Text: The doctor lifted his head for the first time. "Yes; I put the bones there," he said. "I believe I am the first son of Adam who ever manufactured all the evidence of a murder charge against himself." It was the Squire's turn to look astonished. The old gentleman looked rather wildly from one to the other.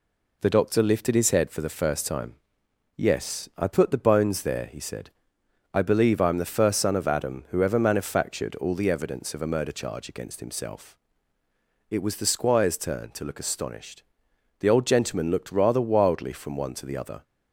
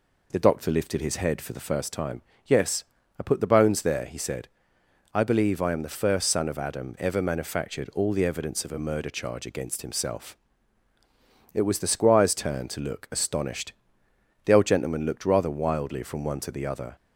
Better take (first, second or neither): first